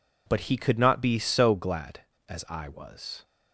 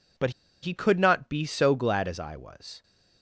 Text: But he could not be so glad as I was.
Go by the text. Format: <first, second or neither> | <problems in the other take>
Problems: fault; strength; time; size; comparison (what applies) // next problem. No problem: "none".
first | pauses between "But" and "he"; slight; at 0.3 s; 0.31 s long